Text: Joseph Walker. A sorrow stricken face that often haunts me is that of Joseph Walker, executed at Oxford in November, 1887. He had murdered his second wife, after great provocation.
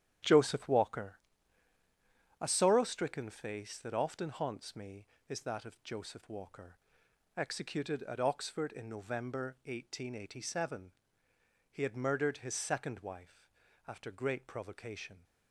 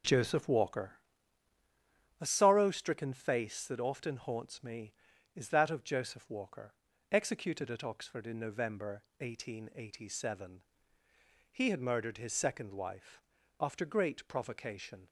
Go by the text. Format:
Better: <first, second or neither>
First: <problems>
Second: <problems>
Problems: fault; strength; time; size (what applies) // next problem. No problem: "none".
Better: second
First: gets quieter; strong; throughout; 9.5 dB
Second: none